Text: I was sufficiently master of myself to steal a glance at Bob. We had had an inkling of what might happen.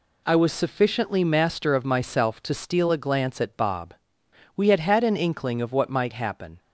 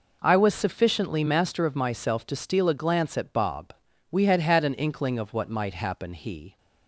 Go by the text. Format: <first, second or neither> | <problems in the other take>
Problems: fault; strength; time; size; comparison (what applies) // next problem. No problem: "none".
first | goes on to say "He"; slight; from 6.1 s on; 0.44 s long